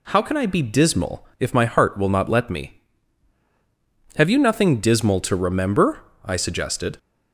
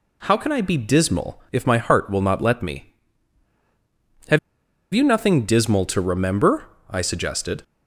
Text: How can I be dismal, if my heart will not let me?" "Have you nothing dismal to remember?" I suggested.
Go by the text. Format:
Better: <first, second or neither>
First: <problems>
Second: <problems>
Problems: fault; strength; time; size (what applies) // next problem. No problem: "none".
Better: first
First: none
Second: pauses between "Have" and "you"; noticeable; at 4.3 s; 0.52 s long